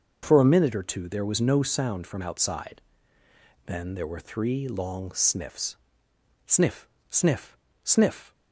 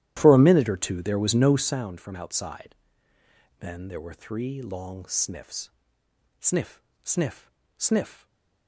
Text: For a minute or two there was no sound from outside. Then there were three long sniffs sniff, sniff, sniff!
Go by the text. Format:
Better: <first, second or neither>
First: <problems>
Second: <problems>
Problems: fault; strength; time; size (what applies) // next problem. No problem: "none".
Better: first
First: pauses between "sniffs" and "sniff"; noticeable; at 5.7 s; 0.70 s long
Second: starts louder than the rest; strong; until 1.9 s; 12.5 dB // pauses between "sniffs" and "sniff"; noticeable; at 5.6 s; 0.70 s long // stays silent after the last word; slight; from 8.1 s on; 0.5 s long